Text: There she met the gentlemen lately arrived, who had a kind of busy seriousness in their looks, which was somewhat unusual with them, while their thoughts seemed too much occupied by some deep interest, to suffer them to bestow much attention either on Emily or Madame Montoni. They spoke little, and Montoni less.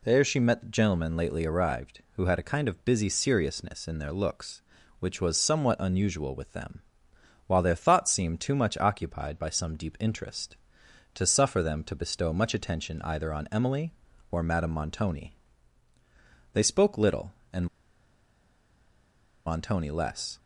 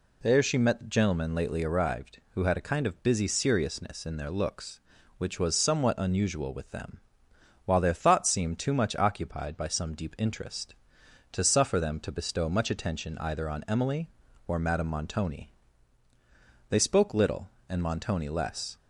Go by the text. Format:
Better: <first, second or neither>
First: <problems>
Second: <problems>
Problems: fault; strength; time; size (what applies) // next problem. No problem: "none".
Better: second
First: pauses between "and" and "Montoni"; strong; at 17.6 s; 1.8 s long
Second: none